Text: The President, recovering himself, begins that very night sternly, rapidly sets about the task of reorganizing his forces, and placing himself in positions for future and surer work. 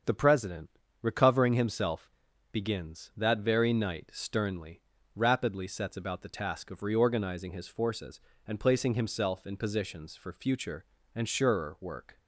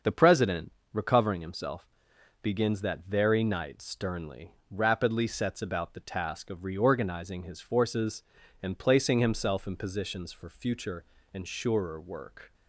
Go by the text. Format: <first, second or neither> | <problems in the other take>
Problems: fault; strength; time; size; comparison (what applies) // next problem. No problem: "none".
neither | starts louder than the rest; the same in both